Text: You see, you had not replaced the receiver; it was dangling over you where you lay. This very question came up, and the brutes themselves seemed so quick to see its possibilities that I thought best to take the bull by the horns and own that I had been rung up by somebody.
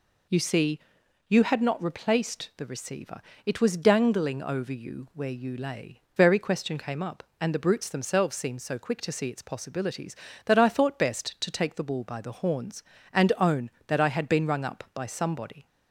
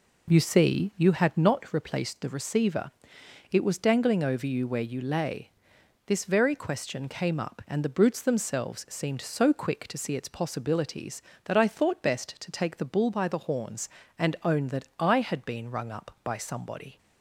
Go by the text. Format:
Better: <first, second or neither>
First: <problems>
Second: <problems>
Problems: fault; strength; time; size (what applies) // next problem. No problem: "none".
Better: second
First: skips "This"; at 6.0 s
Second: none